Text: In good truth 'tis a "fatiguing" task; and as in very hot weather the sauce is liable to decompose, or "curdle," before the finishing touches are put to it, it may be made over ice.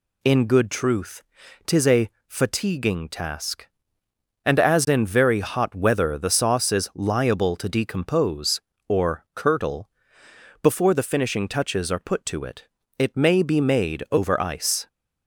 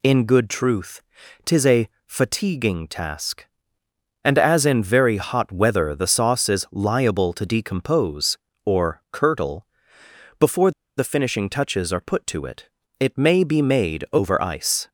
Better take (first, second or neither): first